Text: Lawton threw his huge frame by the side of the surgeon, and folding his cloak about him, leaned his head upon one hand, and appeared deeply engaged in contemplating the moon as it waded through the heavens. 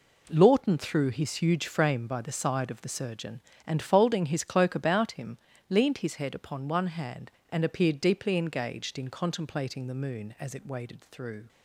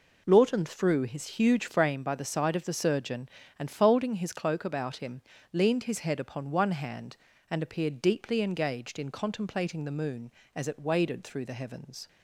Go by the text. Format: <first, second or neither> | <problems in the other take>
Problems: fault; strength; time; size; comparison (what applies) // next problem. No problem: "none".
second | stops before "the heavens"; at 11.4 s